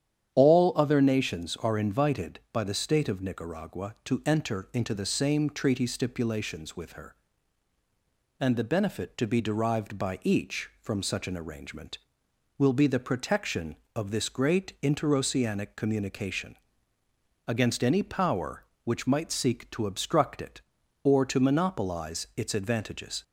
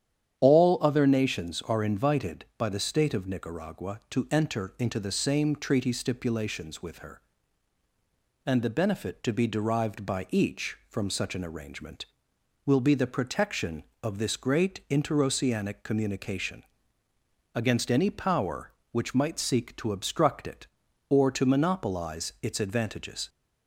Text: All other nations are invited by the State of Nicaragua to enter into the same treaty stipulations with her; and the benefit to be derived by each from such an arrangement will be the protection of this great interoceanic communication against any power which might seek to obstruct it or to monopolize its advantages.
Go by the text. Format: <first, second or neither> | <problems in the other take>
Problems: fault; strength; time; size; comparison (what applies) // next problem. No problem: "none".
neither | starts louder than the rest; strong; the same in both // pauses between "communication" and "against"; noticeable; the same in both